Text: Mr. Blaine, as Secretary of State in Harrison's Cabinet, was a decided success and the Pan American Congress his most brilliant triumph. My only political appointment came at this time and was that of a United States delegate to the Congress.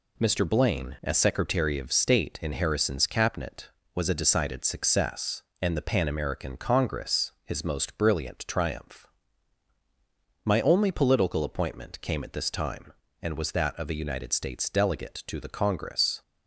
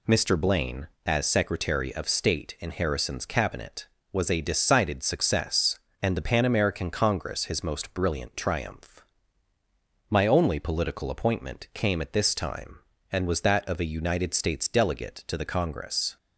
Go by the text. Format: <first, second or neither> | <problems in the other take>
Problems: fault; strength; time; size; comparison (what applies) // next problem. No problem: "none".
neither | none